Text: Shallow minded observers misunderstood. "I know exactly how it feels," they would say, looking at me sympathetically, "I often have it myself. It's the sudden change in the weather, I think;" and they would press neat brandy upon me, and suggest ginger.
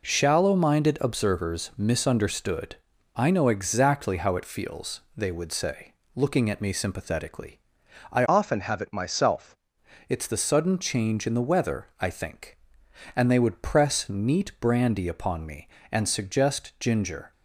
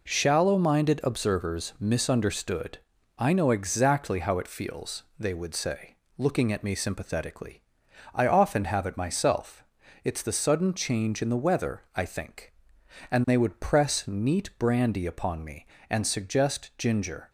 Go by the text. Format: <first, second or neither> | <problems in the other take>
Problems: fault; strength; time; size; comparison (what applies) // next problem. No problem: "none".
second | changes voice from "often" to "myself"; from 8.2 to 9.5 s; 1.3 s long